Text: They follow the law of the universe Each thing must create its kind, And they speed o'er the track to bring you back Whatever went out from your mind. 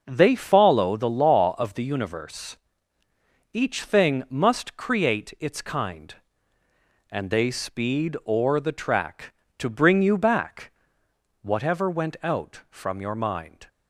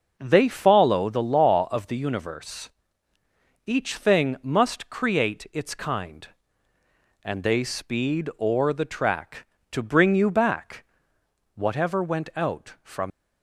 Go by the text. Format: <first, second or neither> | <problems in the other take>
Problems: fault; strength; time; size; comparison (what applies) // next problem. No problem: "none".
first | pauses between "universe" and "Each"; noticeable; at 2.7 s; 0.96 s long; noticeable in the first // pauses between "back" and "Whatever"; noticeable; at 10.8 s; 0.70 s long; noticeable in the first // stops before "your mind"; at 13.1 s